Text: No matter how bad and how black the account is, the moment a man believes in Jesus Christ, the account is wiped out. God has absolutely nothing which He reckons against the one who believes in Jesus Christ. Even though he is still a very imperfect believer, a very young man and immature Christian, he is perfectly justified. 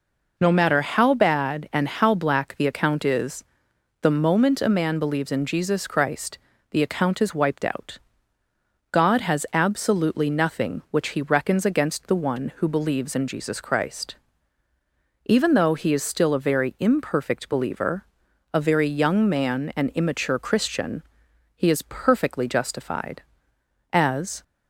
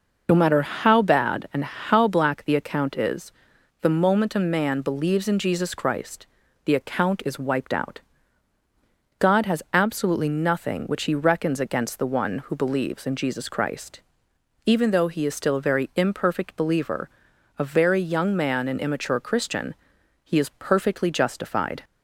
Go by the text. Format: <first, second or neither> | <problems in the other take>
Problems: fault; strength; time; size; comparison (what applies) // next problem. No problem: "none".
second | goes on to say "As"; from 23.9 s on; 0.52 s long